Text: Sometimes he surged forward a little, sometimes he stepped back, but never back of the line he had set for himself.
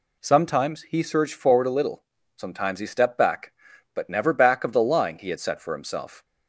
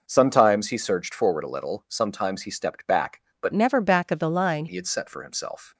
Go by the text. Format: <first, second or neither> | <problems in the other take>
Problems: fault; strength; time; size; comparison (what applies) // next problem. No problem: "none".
first | changes voice from "never" to "line"; from 3.5 to 4.6 s; 1.1 s long